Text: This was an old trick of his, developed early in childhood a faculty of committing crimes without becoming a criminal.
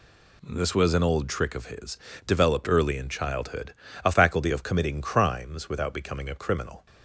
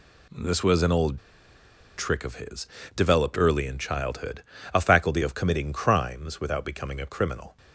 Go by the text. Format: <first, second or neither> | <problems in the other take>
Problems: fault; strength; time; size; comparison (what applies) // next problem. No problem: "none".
first | pauses between "old" and "trick"; noticeable; at 1.1 s; 0.79 s long // pauses between "childhood" and "a"; slight; at 4.4 s; 0.32 s long; slight in the first